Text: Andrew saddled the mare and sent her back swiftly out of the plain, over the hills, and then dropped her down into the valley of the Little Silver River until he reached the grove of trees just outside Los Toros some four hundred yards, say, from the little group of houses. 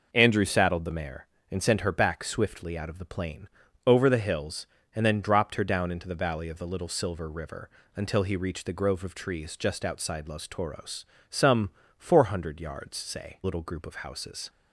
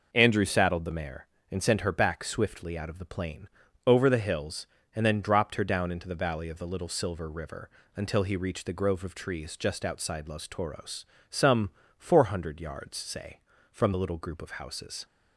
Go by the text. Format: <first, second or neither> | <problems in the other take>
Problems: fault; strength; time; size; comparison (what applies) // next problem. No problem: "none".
second | pauses between "River" and "until"; slight; at 7.6 s; 0.26 s long; slight in the second // pauses between "Toros" and "some"; slight; at 11.0 s; 0.24 s long; slight in the second // pauses between "some" and "four"; slight; at 11.6 s; 0.28 s long; slight in the second // skips "from the"; at 13.4 s